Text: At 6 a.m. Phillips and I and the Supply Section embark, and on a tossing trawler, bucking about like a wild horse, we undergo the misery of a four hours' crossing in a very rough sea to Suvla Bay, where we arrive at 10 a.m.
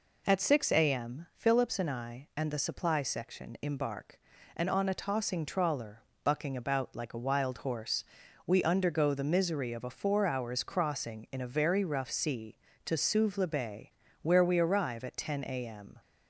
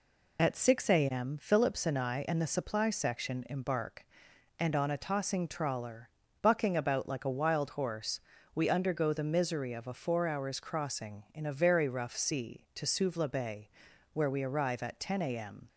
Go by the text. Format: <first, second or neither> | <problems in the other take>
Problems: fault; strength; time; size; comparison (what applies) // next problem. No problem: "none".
neither | none